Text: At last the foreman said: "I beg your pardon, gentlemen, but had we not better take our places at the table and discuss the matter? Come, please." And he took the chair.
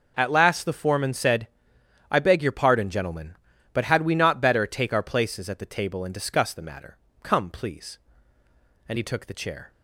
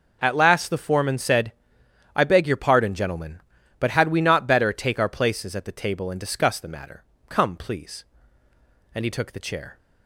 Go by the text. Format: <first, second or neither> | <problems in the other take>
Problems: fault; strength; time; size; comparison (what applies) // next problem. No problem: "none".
neither | none